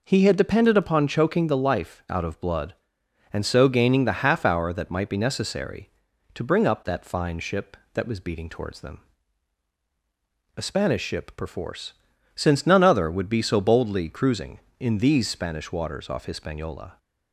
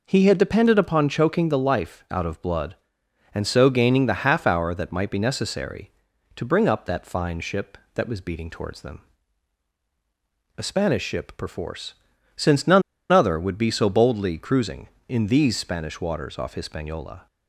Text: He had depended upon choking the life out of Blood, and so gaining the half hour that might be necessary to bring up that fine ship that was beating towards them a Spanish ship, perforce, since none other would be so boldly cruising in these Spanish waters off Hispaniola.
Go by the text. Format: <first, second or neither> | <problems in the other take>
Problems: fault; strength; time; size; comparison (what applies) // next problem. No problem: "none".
first | pauses between "them" and "a"; strong; at 9.0 s; 1.5 s long; strong in the first // pauses between "none" and "other"; slight; at 12.8 s; 0.30 s long